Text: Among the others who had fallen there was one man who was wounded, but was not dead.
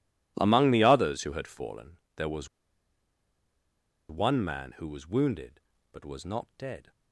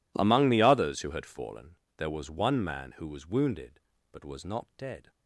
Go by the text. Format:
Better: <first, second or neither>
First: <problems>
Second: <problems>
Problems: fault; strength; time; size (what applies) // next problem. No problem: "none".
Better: second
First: pauses between "fallen" and "there"; slight; at 1.9 s; 0.20 s long // pauses between "was" and "one"; strong; at 2.4 s; 1.6 s long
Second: pauses between "fallen" and "there"; slight; at 1.7 s; 0.22 s long